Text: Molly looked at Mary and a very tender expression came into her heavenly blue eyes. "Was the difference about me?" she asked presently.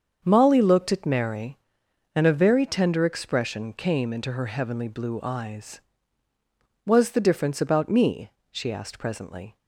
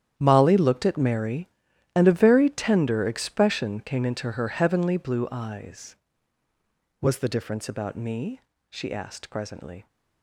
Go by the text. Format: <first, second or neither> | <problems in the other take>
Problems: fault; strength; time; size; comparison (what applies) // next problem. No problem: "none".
first | gets quieter; strong; throughout; 15 dB // starts louder than the rest; strong; until 1.1 s; 10 dB; also in the first